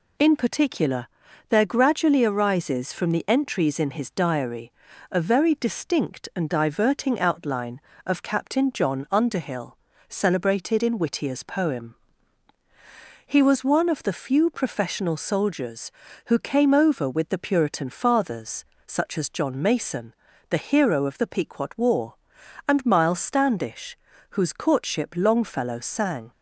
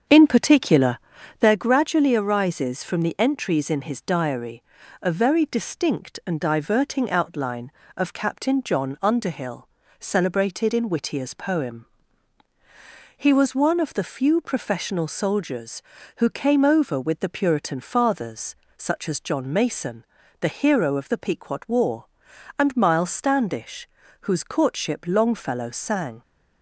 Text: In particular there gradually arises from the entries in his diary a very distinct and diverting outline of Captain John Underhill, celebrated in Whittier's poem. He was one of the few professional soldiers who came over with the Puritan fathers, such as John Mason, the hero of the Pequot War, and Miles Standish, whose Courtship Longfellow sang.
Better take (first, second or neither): first